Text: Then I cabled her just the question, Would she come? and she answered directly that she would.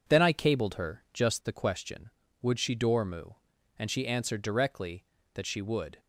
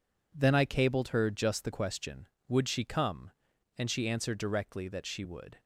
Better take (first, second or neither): second